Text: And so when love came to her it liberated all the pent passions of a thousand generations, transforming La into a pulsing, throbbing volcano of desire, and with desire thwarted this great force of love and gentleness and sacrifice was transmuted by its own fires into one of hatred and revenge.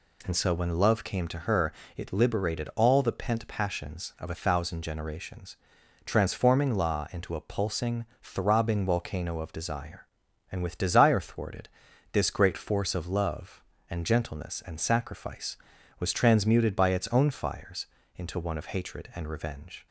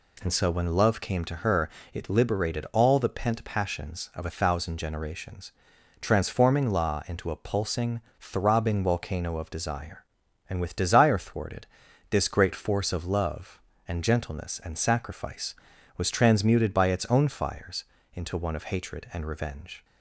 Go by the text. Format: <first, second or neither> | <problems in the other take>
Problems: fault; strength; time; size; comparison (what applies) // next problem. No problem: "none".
neither | pauses between "her" and "it"; slight; the same in both // pauses between "thwarted" and "this"; the same in both // pauses between "fires" and "into"; slight; the same in both